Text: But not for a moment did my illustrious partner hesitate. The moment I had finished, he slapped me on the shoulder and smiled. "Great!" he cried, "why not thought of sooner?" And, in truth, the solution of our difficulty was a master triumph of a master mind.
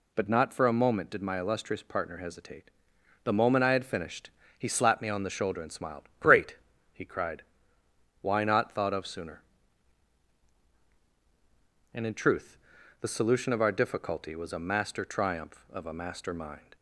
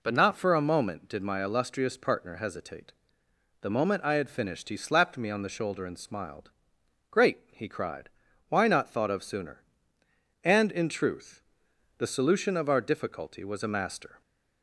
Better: first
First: none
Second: stops before "triumph of a master mind"; at 14.2 s

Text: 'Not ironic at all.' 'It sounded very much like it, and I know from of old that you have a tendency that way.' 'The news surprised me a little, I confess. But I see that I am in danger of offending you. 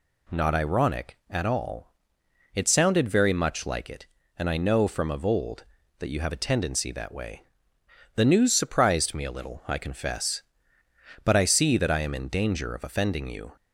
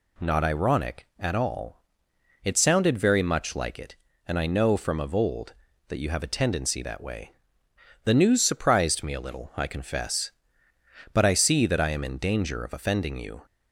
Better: neither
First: none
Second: none

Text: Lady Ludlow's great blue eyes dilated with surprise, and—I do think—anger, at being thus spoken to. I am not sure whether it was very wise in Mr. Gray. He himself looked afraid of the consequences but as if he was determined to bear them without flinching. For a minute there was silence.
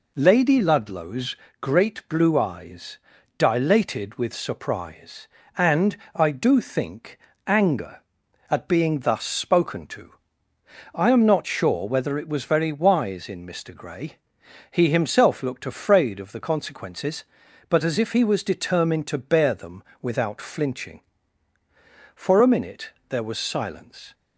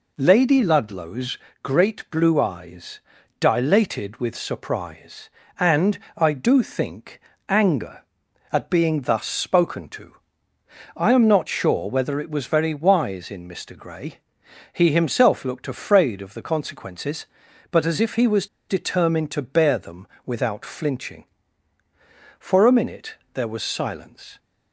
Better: first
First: pauses between "Ludlow's" and "great"; slight; at 1.3 s; 0.24 s long // pauses between "eyes" and "dilated"; at 2.9 s; 0.40 s long // pauses between "them" and "without"; slight; at 19.8 s; 0.18 s long // pauses between "minute" and "there"; slight; at 22.8 s; 0.20 s long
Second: pauses between "Ludlow's" and "great"; slight; at 1.3 s; 0.24 s long // pauses between "eyes" and "dilated"; at 2.9 s; 0.40 s long // pauses between "was" and "determined"; slight; at 18.4 s; 0.23 s long // pauses between "them" and "without"; slight; at 20.0 s; 0.18 s long // pauses between "minute" and "there"; slight; at 23.1 s; 0.20 s long

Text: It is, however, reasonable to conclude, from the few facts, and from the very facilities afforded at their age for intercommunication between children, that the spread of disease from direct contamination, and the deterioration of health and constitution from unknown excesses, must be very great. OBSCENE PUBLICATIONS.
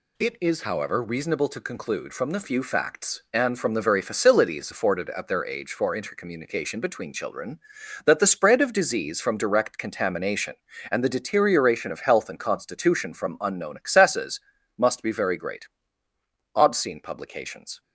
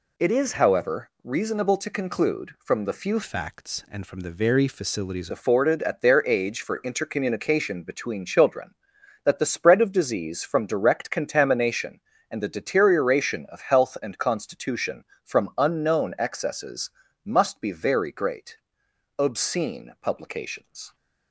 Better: first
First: none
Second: changes voice from "facts" to "facilities"; from 3.2 to 5.3 s; 2.1 s long

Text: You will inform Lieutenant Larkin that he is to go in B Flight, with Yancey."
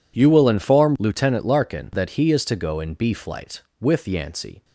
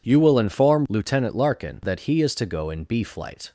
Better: first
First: none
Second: stops before "with Yancey"; at 3.4 s

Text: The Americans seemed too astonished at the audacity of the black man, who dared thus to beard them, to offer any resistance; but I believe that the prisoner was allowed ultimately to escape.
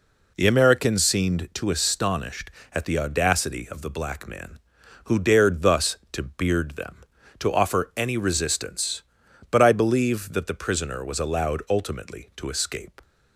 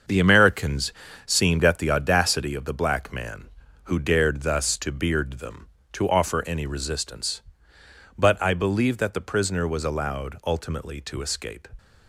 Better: first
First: none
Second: starts louder than the rest; until 1.4 s; 6.5 dB // pauses between "Americans" and "seemed"; slight; at 0.9 s; 0.34 s long // skips "too astonished"; at 1.6 s

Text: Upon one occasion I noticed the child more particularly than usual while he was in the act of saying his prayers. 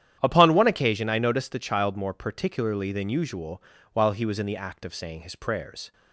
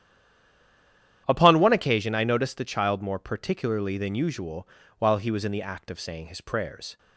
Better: first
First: starts louder than the rest; strong; until 1.2 s; 10.5 dB // pauses between "usual" and "while"; slight; at 3.6 s; 0.30 s long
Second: stays silent before the first word; noticeable; until 1.2 s; 1.2 s long // starts louder than the rest; strong; until 2.2 s; 10.5 dB // pauses between "usual" and "while"; slight; at 4.6 s; 0.30 s long

